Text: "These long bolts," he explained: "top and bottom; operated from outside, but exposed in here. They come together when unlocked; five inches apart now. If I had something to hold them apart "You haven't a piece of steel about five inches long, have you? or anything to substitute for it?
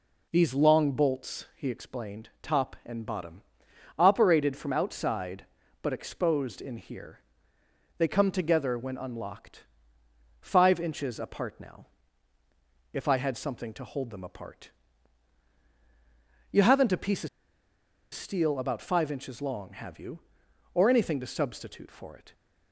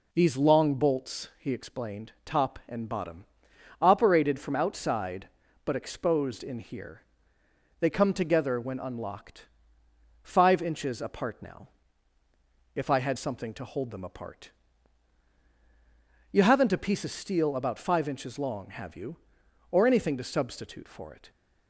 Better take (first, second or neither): second